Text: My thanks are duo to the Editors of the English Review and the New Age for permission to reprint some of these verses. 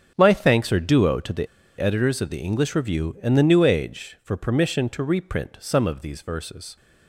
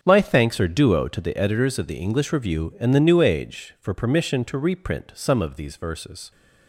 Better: second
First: starts louder than the rest; strong; until 1.1 s; 7 dB // pauses between "the" and "Editors"; slight; at 1.4 s; 0.32 s long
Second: starts louder than the rest; until 1.0 s; 7 dB

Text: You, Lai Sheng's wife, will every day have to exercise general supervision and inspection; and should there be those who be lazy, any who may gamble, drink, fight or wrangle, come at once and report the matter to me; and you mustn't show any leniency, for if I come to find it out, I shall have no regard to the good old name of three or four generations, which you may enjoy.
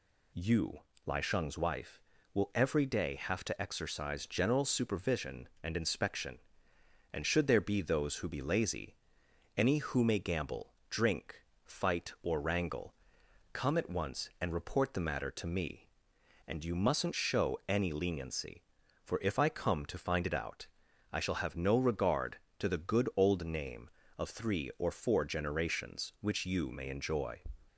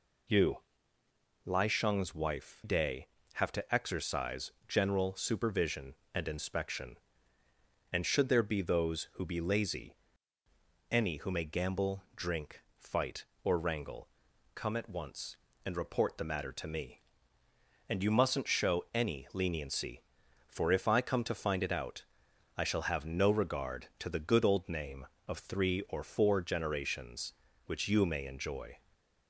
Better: first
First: none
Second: skips "will every"; at 2.6 s // pauses between "exercise" and "general"; slight; at 4.5 s; 0.16 s long // stays silent after the last word; slight; from 28.7 s on; 0.5 s long

